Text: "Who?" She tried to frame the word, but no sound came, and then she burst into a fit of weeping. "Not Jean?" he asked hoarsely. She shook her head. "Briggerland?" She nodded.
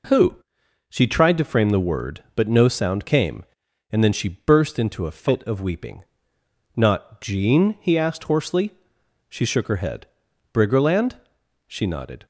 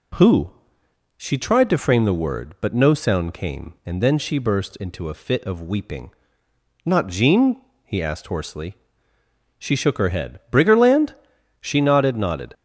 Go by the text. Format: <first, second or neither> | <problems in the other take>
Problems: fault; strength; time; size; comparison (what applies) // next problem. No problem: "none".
first | says "nodded" twice; at 12.1 s